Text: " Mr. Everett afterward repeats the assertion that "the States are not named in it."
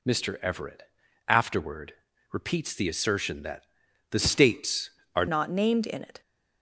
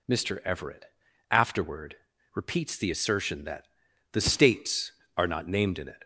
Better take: second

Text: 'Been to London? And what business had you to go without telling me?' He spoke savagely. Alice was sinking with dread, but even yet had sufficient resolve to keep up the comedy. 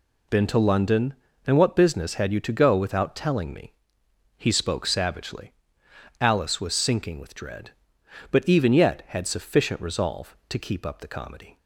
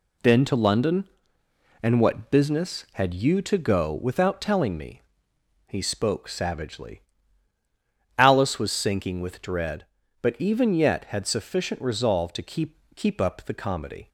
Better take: first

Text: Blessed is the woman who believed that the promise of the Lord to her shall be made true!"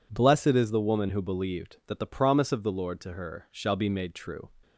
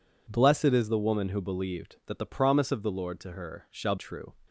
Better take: first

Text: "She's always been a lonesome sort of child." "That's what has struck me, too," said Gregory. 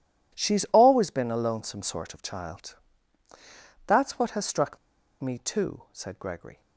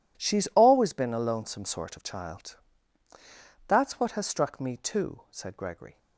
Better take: second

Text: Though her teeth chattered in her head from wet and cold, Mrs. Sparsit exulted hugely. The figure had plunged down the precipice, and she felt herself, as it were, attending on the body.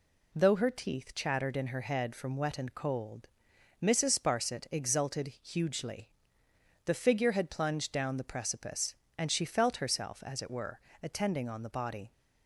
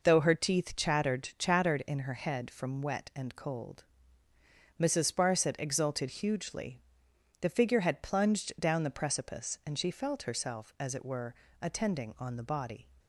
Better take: first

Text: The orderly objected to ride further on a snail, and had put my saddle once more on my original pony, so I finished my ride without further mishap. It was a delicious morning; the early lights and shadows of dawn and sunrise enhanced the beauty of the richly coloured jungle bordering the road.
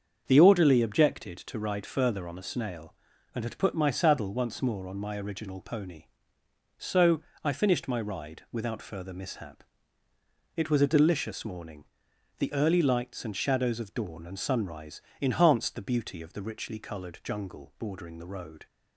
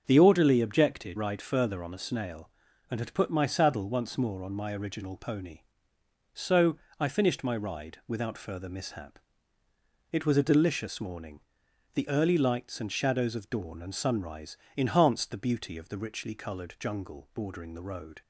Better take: first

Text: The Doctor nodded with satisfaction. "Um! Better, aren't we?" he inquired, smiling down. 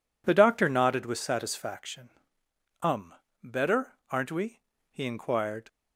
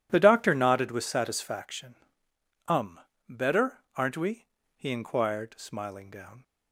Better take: second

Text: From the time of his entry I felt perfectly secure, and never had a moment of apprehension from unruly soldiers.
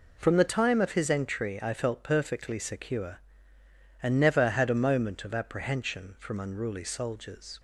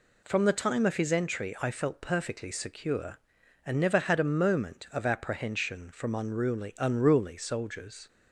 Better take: first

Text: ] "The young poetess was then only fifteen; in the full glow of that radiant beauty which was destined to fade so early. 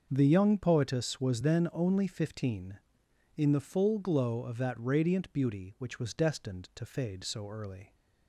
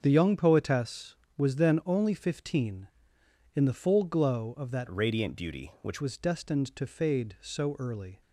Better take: first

